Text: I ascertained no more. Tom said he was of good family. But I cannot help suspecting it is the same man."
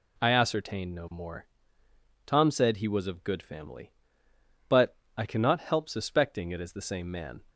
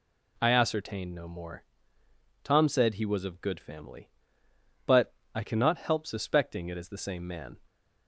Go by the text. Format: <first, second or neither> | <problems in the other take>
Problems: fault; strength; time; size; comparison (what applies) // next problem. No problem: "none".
neither | pauses between "But" and "I"; slight; the same in both